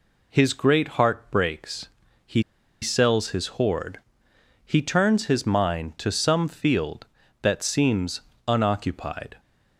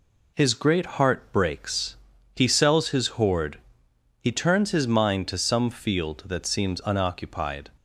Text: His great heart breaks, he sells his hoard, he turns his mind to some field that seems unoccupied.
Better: second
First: pauses between "he" and "sells"; at 2.4 s; 0.41 s long // pauses between "seems" and "unoccupied"; slight; at 8.2 s; 0.26 s long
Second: none

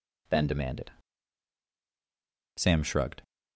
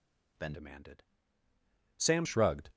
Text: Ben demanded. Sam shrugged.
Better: first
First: none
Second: changes voice from "demanded" to "Sam"; from 0.5 to 2.2 s; 1.7 s long

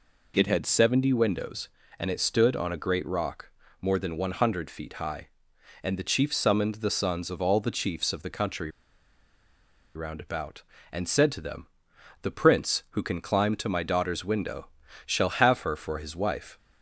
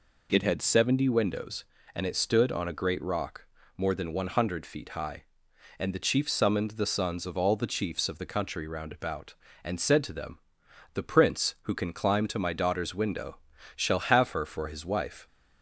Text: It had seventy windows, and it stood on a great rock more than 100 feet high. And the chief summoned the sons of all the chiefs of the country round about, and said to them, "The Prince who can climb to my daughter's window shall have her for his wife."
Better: second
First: pauses between "rock" and "more"; slight; at 3.5 s; 0.30 s long // pauses between "country" and "round"; strong; at 8.6 s; 1.2 s long // pauses between "window" and "shall"; slight; at 14.6 s; 0.36 s long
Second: pauses between "rock" and "more"; slight; at 3.4 s; 0.30 s long // pauses between "window" and "shall"; slight; at 13.3 s; 0.36 s long

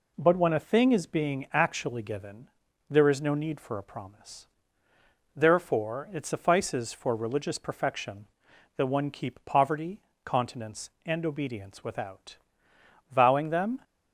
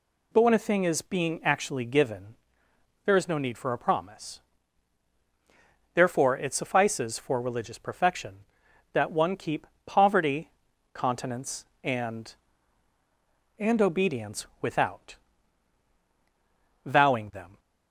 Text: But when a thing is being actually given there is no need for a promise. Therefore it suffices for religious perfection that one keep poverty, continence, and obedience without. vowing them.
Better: first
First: pauses between "given" and "there"; at 2.4 s; 0.42 s long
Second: pauses between "given" and "there"; noticeable; at 2.3 s; 0.70 s long // pauses between "keep" and "poverty"; slight; at 9.6 s; 0.20 s long // says "and" twice; at 13.5 s

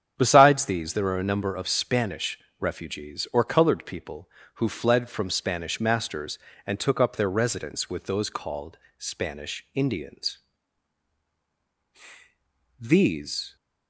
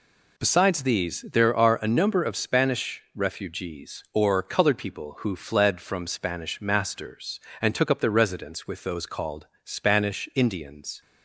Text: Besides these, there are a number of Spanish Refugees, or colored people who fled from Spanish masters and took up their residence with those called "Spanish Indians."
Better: second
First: starts louder than the rest; strong; until 1.2 s; 8.5 dB // pauses between "Spanish" and "Refugees"; slight; at 2.3 s; 0.18 s long // pauses between "called" and "Spanish"; slight; at 8.7 s; 0.20 s long // goes on to say "These"; noticeable; from 12.7 s on; 0.76 s long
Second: pauses between "called" and "Spanish"; slight; at 9.4 s; 0.18 s long

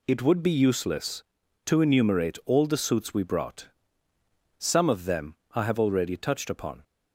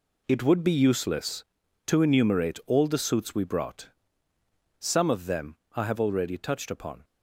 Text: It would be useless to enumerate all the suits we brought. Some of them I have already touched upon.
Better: first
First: pauses between "them" and "I"; slight; at 5.3 s; 0.20 s long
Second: gets quieter; strong; throughout; 10.5 dB // pauses between "them" and "I"; slight; at 5.5 s; 0.20 s long

